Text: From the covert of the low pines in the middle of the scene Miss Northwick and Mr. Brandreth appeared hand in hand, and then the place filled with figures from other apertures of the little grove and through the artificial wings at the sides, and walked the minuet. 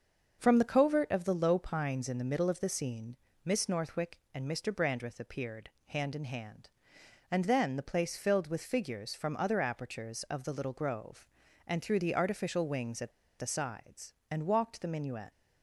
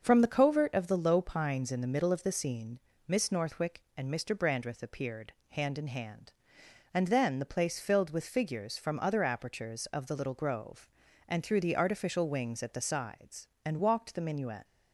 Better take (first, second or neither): second